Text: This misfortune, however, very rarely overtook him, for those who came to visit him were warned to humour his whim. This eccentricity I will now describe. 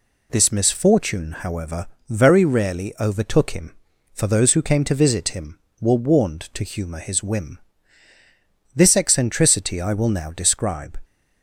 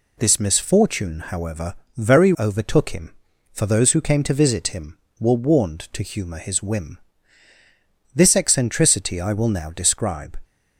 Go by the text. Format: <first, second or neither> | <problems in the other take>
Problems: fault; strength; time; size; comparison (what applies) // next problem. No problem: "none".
first | skips "rarely"; at 2.3 s